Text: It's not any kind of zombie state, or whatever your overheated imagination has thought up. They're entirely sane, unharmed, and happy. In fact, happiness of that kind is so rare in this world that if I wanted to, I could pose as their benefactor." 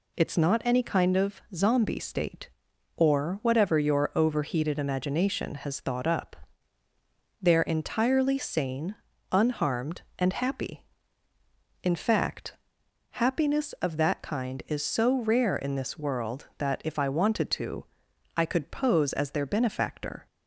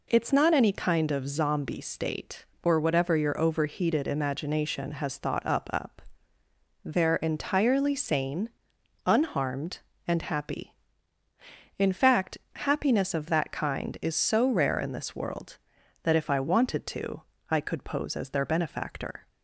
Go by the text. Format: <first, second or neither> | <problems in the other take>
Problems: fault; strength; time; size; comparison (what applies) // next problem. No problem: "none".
first | says "up" twice; at 5.7 s